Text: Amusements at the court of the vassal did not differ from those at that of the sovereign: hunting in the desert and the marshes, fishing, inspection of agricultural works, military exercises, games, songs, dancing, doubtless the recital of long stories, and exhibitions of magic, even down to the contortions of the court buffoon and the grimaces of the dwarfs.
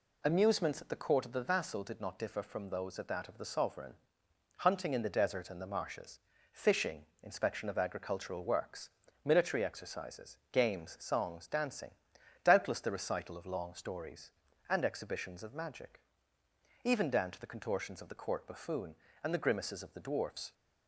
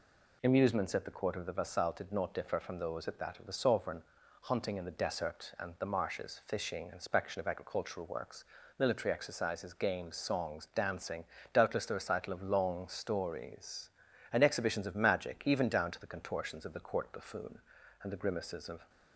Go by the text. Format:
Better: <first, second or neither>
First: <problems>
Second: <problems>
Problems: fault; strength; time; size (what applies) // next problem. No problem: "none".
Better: first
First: none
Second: stops before "the dwarfs"; at 18.8 s